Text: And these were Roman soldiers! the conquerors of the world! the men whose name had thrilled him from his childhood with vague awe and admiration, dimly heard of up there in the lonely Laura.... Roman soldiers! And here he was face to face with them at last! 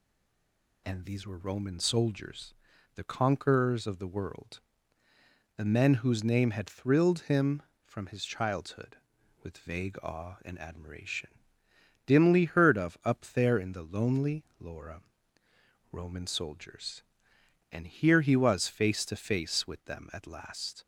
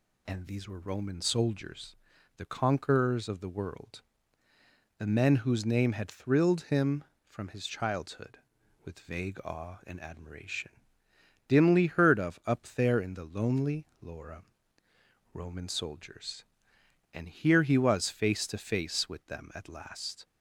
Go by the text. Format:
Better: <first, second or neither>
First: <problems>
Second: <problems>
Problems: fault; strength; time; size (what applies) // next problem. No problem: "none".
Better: second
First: stays silent before the first word; slight; until 0.8 s; 0.8 s long // pauses between "lonely" and "Laura"; slight; at 14.4 s; 0.16 s long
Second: pauses between "lonely" and "Laura"; slight; at 13.8 s; 0.16 s long